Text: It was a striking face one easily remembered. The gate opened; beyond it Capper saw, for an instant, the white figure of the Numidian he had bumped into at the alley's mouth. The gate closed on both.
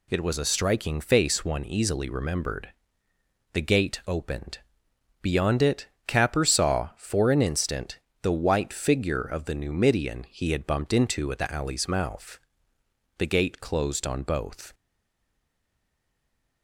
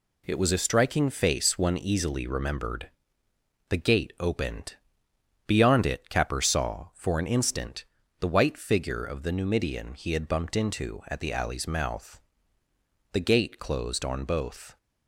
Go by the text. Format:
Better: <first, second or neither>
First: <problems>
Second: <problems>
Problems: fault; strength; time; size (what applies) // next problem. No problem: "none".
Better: second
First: pauses between "it" and "Capper"; slight; at 5.8 s; 0.20 s long // stays silent after the last word; noticeable; from 14.7 s on; 1.9 s long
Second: none